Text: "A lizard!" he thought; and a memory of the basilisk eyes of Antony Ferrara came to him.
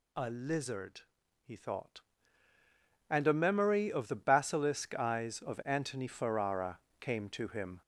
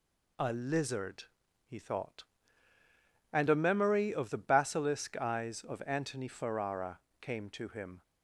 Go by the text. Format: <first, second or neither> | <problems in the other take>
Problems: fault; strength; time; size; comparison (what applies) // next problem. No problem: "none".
second | gets louder; noticeable; throughout; 4.5 dB // pauses between "Ferrara" and "came"; slight; at 6.7 s; 0.22 s long; slight in the second